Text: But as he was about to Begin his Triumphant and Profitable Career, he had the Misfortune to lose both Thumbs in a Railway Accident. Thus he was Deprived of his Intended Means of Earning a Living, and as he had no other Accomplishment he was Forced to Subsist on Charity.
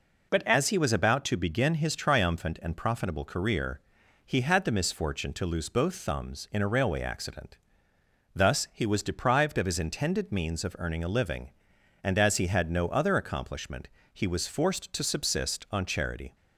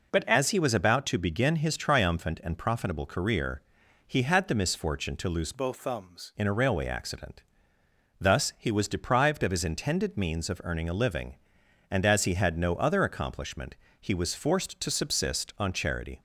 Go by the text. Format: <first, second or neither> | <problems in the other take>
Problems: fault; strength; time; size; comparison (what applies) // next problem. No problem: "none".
first | changes voice from "both" to "Thumbs"; from 5.5 to 6.3 s; 0.8 s long // pauses between "Accomplishment" and "he"; slight; at 13.7 s; 0.26 s long; slight in the first